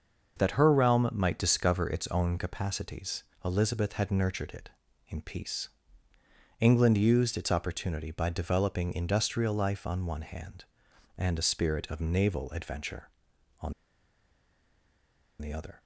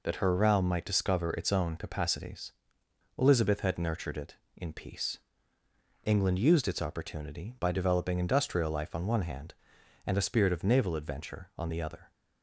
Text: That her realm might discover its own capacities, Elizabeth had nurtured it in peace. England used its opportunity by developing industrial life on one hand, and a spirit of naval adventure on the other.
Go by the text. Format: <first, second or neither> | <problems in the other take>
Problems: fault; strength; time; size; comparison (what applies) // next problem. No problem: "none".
second | starts louder than the rest; noticeable; until 1.4 s; 6 dB // pauses between "on" and "the"; strong; at 13.7 s; 1.6 s long